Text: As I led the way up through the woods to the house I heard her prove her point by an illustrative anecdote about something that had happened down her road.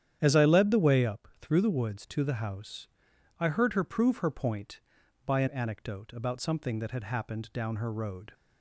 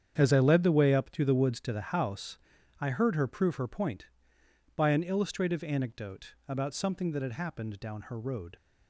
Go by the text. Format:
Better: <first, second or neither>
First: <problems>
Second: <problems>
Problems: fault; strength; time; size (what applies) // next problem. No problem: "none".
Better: second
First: starts louder than the rest; strong; until 1.2 s; 9.5 dB // pauses between "house" and "I"; noticeable; at 2.8 s; 0.52 s long // skips "illustrative"; at 5.4 s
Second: starts louder than the rest; strong; until 1.1 s; 8 dB // pauses between "house" and "I"; at 2.3 s; 0.41 s long